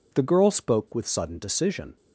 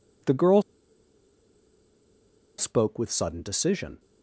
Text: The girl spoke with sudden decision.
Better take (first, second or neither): first